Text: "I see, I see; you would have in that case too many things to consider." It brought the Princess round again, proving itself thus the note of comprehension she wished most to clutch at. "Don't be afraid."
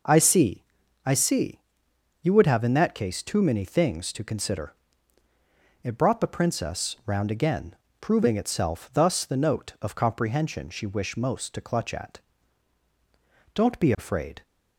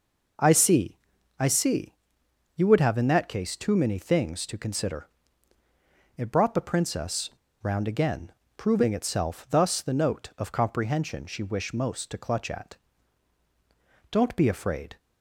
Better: first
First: none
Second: pauses between "Princess" and "round"; slight; at 7.3 s; 0.32 s long

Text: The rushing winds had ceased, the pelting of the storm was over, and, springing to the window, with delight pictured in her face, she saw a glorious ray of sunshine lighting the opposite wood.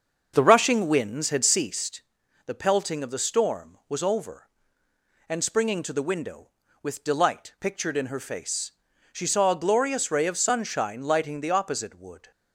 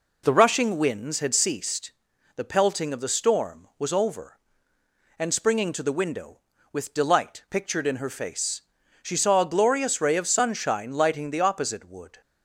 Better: second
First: starts louder than the rest; until 1.8 s; 6.5 dB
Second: none

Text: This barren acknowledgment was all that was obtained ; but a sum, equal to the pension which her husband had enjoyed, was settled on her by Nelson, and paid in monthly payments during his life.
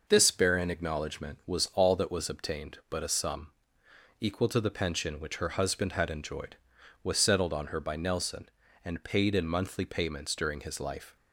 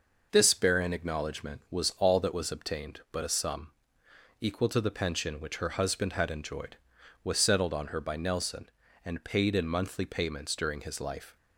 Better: neither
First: none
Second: none

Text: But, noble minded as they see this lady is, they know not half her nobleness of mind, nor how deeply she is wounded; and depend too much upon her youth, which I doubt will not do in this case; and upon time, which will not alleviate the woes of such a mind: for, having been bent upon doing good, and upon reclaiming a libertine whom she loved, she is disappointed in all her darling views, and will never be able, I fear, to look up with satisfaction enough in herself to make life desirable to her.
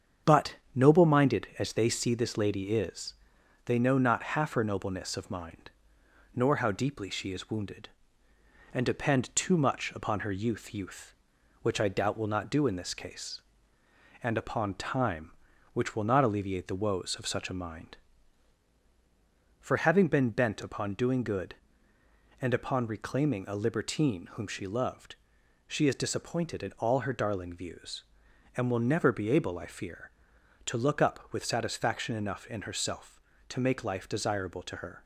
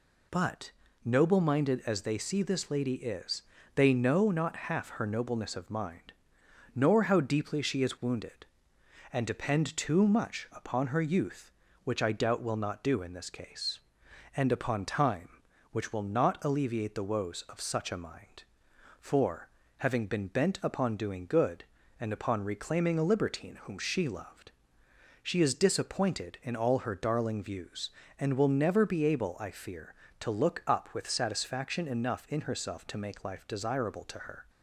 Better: second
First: starts louder than the rest; strong; until 1.4 s; 7.5 dB // says "youth" twice; at 10.7 s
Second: none

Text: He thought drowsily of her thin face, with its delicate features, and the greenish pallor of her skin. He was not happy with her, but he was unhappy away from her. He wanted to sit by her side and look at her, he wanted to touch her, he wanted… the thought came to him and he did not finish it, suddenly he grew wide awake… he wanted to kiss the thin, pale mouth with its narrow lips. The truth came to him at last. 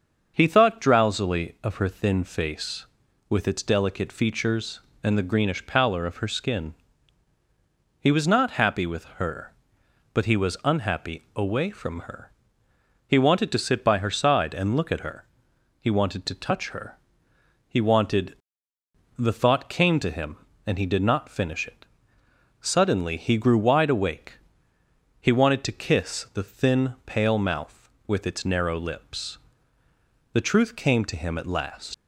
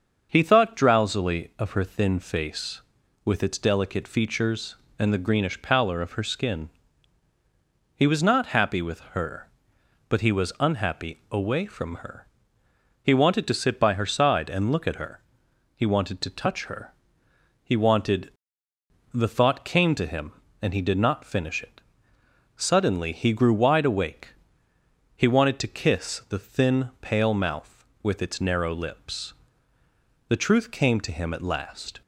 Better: second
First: starts louder than the rest; until 1.3 s; 6.5 dB // leaves "last" unfinished; at 31.9 s; 115 ms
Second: starts louder than the rest; until 1.3 s; 6.5 dB

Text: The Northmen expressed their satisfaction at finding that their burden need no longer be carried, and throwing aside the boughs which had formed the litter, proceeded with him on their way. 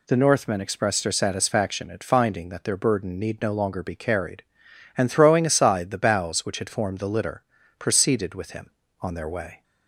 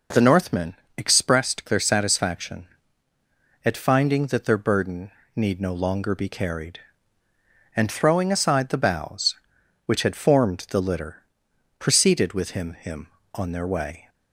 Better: first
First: none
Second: pauses between "Northmen" and "expressed"; slight; at 0.7 s; 0.22 s long // pauses between "burden" and "need"; slight; at 5.0 s; 0.28 s long // says "him" twice; at 12.7 s

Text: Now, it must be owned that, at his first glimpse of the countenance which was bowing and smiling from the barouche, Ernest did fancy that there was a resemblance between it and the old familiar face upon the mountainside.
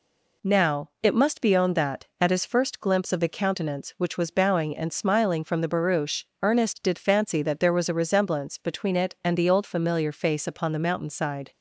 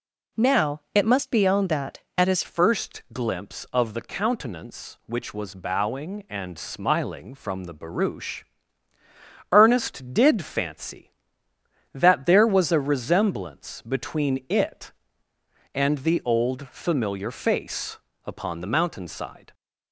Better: first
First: none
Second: changes voice at "first"; from 2.4 s on; 17.1 s long // pauses between "face" and "upon"; slight; at 17.9 s; 0.28 s long

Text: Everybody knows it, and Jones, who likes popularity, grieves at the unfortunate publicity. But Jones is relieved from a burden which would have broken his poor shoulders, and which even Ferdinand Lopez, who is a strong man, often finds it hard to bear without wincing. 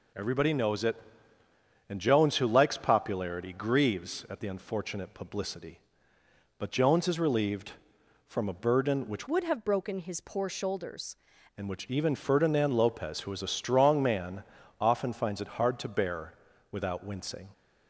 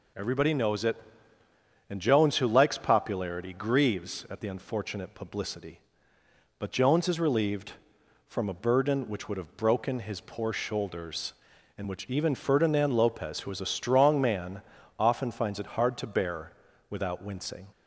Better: second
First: changes voice from "would" to "shoulders"; from 9.2 to 11.1 s; 1.9 s long // pauses between "bear" and "without"; at 16.3 s; 0.38 s long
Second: pauses between "bear" and "without"; at 16.5 s; 0.38 s long

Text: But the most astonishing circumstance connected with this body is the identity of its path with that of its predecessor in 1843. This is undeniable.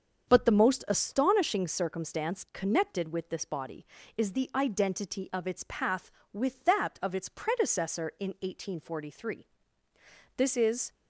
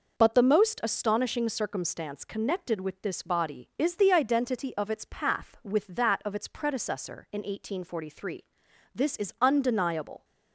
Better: second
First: starts louder than the rest; until 1.3 s; 7 dB // stops before "undeniable"; at 10.9 s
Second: none

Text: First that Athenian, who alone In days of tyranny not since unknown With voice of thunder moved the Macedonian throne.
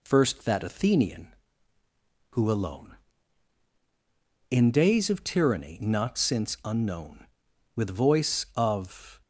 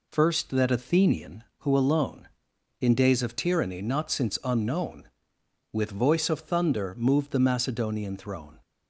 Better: second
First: stops before "thunder moved the Macedonian throne"; at 9.2 s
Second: none

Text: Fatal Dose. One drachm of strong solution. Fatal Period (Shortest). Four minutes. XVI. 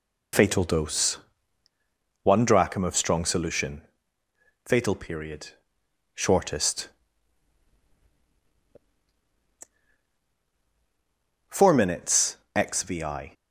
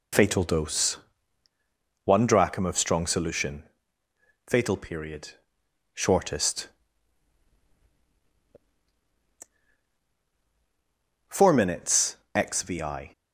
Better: neither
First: none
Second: none

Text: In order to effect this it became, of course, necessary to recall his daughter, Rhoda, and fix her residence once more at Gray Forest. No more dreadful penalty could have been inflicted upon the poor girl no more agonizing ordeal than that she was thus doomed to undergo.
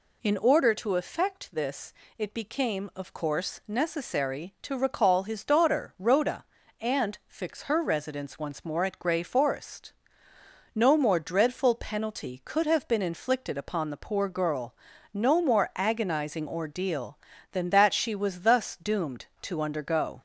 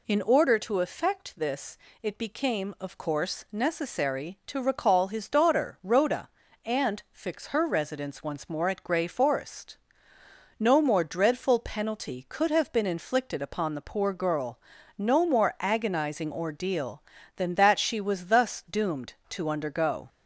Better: neither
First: pauses between "this" and "it"; slight; at 1.9 s; 0.24 s long // pauses between "girl" and "no"; at 14.7 s; 0.38 s long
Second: pauses between "this" and "it"; slight; at 1.7 s; 0.24 s long // pauses between "girl" and "no"; at 14.5 s; 0.38 s long

